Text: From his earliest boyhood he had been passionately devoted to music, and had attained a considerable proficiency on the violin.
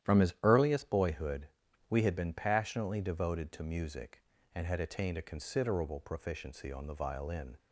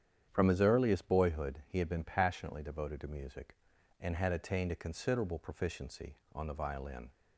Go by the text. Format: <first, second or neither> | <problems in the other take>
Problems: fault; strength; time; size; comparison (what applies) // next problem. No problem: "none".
second | starts louder than the rest; strong; until 1.1 s; 11 dB; strong in the second // says "we" for "he"; at 1.9 s